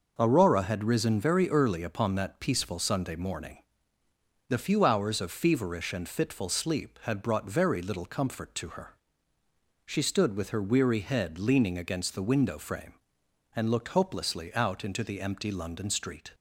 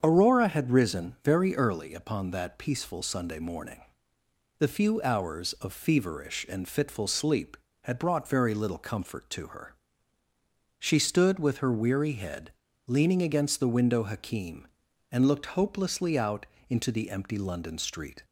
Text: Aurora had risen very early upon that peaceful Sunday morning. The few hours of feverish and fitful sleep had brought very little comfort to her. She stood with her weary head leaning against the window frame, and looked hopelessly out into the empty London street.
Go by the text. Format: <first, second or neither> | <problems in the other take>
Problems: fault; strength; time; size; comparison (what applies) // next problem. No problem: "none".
first | starts louder than the rest; strong; until 1.0 s; 7 dB // pauses between "head" and "leaning"; slight; at 12.5 s; 0.36 s long // says "hakim" for "frame"; at 14.0 s // pauses between "out" and "into"; slight; at 16.4 s; 0.24 s long